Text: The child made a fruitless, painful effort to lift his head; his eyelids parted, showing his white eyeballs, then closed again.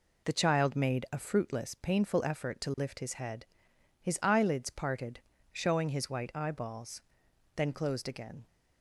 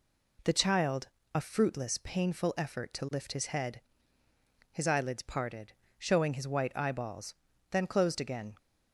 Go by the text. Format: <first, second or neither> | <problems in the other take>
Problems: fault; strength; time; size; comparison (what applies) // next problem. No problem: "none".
first | skips "made"; at 1.2 s